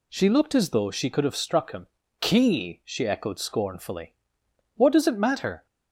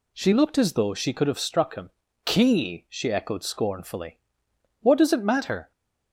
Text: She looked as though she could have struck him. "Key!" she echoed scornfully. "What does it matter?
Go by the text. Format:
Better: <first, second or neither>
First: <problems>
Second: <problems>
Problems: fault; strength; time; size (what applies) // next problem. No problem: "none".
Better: neither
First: none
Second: none